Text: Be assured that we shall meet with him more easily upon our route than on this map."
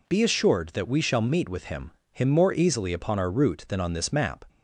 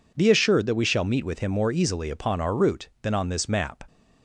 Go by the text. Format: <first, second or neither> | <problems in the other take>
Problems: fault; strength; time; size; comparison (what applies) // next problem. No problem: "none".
second | says "him" twice; at 2.1 s